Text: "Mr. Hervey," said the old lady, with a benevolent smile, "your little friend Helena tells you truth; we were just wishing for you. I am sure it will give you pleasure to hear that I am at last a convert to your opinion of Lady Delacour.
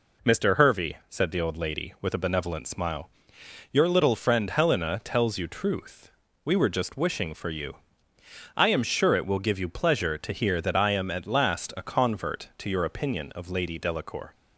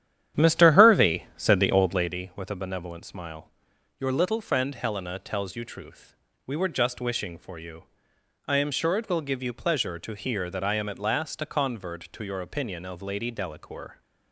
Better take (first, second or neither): first